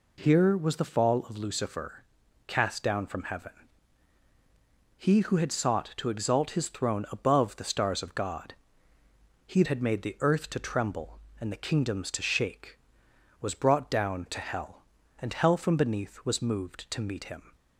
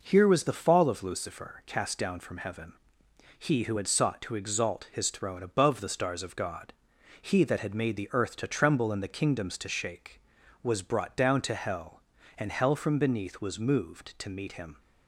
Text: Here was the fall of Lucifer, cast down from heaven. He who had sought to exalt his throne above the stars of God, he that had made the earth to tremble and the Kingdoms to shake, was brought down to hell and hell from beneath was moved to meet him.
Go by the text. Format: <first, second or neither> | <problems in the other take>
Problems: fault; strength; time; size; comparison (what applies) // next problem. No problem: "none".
second | skips "that"; at 9.6 s